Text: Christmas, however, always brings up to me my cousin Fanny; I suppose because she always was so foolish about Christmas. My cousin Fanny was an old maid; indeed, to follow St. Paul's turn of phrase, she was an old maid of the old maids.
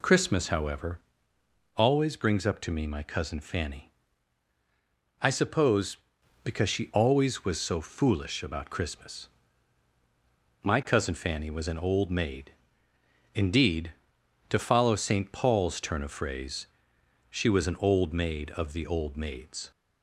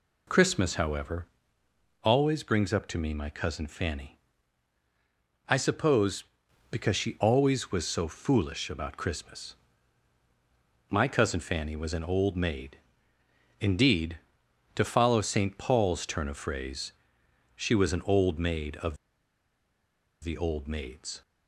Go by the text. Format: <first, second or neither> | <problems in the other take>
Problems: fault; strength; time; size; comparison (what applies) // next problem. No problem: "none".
first | pauses between "of" and "the"; strong; at 18.9 s; 1.2 s long